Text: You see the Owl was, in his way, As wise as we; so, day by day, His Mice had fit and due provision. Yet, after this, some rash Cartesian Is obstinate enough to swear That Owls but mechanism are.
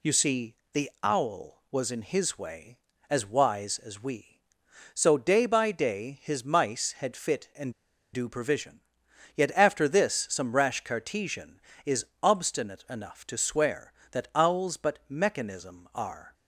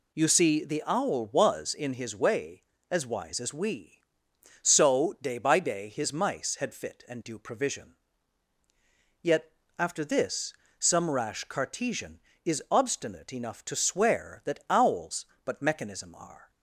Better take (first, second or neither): second